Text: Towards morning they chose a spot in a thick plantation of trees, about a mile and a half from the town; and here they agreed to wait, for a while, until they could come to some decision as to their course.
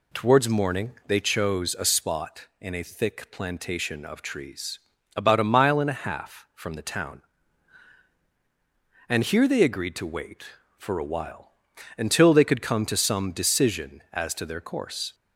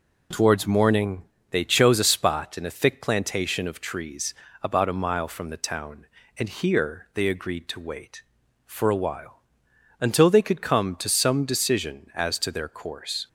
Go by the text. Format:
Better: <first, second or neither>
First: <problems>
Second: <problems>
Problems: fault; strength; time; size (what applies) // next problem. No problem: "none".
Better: first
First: none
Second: pauses between "morning" and "they"; slight; at 1.2 s; 0.24 s long // skips "and a half"; at 5.2 s